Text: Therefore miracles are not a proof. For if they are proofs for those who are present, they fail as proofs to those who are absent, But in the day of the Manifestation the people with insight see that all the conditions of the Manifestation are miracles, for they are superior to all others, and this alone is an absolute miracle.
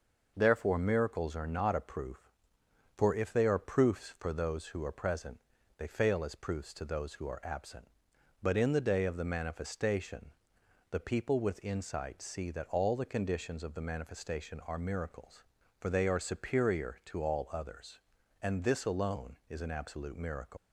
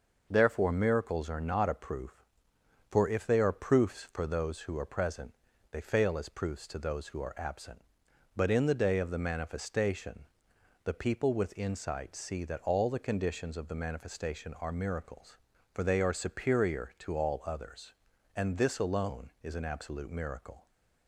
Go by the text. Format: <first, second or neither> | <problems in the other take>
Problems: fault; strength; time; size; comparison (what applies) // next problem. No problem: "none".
second | pauses between "Manifestation" and "the"; noticeable; at 10.2 s; 0.60 s long; noticeable in the second // leaves "miracle" unfinished; at 20.5 s; 145 ms